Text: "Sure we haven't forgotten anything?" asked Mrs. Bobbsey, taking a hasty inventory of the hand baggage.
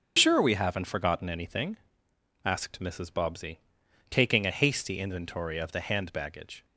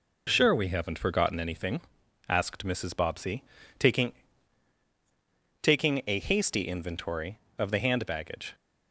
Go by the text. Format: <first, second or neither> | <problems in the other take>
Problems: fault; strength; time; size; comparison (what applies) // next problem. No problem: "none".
first | says "taking" twice; at 5.6 s